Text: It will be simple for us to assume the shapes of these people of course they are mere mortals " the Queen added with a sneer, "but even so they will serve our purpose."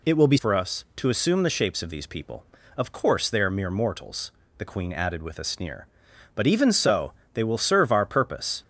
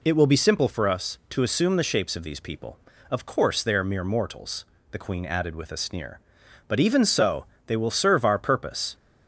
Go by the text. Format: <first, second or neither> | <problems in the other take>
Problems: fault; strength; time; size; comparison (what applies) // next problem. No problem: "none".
second | skips "simple"; at 0.3 s // pauses between "so" and "they"; slight; at 7.1 s; 0.20 s long; slight in the second